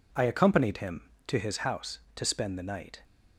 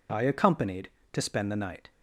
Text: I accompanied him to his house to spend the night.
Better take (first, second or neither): first